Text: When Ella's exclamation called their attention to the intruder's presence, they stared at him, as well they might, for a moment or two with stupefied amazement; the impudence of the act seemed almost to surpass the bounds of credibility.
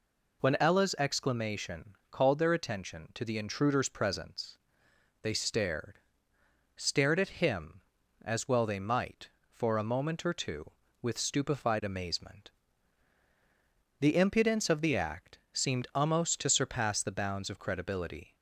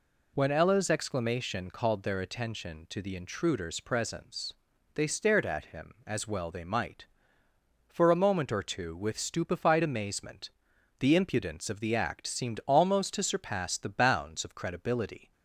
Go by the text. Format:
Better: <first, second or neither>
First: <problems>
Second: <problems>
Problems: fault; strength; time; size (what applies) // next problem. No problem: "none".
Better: second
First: says "stared" twice; at 6.7 s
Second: none